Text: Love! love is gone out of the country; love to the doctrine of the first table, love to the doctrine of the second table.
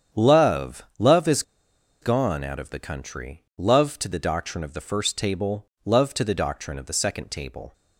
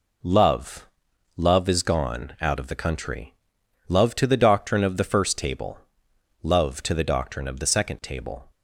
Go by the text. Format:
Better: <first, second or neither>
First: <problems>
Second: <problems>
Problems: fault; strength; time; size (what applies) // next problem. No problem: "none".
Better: second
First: starts louder than the rest; strong; until 1.2 s; 8.5 dB // pauses between "is" and "gone"; noticeable; at 1.4 s; 0.59 s long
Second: none